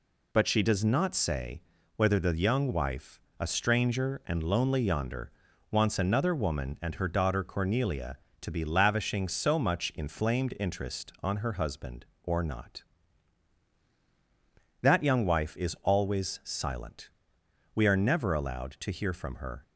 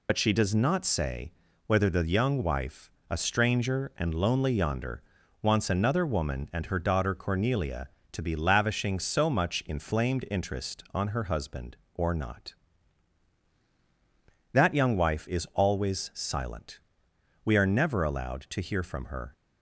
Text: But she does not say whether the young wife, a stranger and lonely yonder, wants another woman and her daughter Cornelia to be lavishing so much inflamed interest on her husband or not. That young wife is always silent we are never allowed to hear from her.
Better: first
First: pauses between "say" and "whether"; slight; at 1.6 s; 0.34 s long // pauses between "silent" and "we"; noticeable; at 17.0 s; 0.64 s long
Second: loses the start of "But"; at 0.0 s; 60 ms // pauses between "say" and "whether"; slight; at 1.3 s; 0.34 s long // pauses between "silent" and "we"; noticeable; at 16.7 s; 0.64 s long

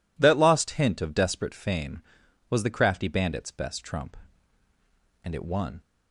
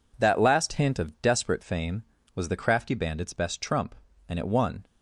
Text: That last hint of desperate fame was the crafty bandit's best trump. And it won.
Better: second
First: says "lost" for "last"; at 0.3 s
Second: none

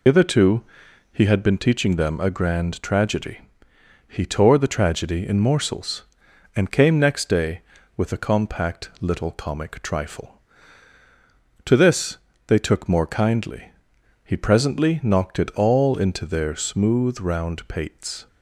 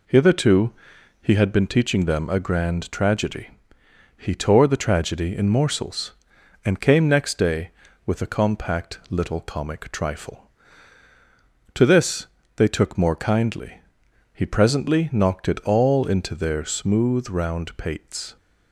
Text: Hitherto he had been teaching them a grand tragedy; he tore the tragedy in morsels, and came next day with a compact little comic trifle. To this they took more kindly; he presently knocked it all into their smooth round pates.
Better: second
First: loses the start of "Hitherto"; at 0.0 s; 90 ms // pauses between "Hitherto" and "he"; noticeable; at 0.6 s; 0.50 s long // pauses between "this" and "they"; slight; at 12.1 s; 0.26 s long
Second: pauses between "Hitherto" and "he"; noticeable; at 0.6 s; 0.50 s long // pauses between "this" and "they"; slight; at 12.2 s; 0.26 s long

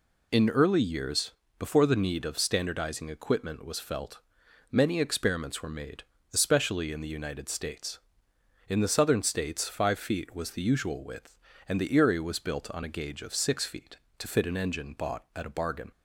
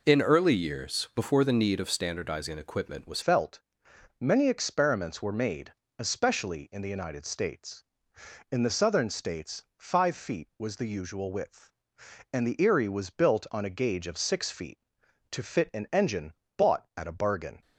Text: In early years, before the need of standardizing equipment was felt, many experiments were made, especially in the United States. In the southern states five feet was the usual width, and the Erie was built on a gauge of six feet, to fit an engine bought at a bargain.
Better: first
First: none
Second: changes voice at "felt"; from 3.2 s on; 14.4 s long // pauses between "states" and "five"; slight; at 9.6 s; 0.16 s long // pauses between "engine" and "bought"; slight; at 16.3 s; 0.24 s long

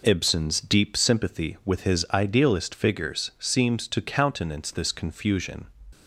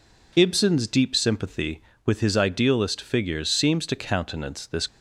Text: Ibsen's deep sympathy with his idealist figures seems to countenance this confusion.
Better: first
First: none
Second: stops before "confusion"; at 4.8 s

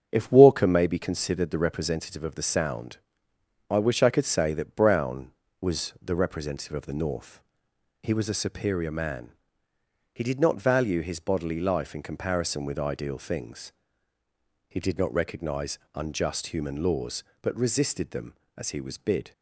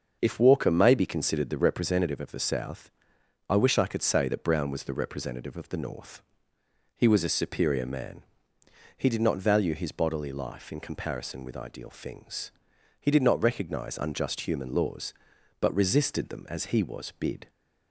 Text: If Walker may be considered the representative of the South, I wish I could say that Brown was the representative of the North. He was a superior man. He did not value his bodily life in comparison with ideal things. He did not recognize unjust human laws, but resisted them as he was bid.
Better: second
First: starts louder than the rest; strong; until 1.1 s; 7.5 dB // says "Sound" for "South"; at 2.4 s // pauses between "recognize" and "unjust"; slight; at 15.7 s; 0.16 s long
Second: starts louder than the rest; until 1.2 s; 6.5 dB

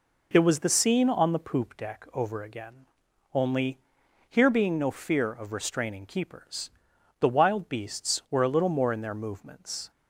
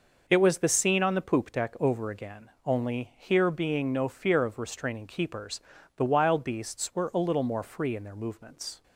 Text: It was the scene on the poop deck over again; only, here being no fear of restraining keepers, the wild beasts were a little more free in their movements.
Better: second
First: skips "free"; at 8.9 s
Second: none

